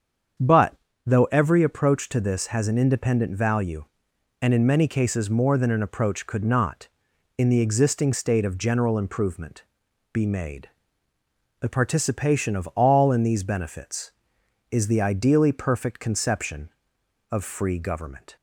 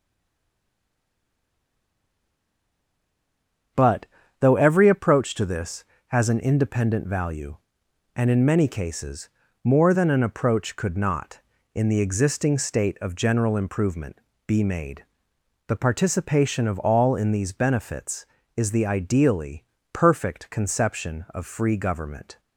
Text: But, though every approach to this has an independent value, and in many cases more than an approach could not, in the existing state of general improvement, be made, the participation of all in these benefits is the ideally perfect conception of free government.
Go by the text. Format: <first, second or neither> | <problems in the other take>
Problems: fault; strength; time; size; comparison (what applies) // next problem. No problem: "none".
first | stays silent before the first word; strong; until 3.7 s; 3.7 s long // starts louder than the rest; until 5.0 s; 7 dB; strong in the first // pauses between "cases" and "more"; slight; at 9.2 s; 0.34 s long // pauses between "ideally" and "perfect"; slight; at 19.6 s; 0.28 s long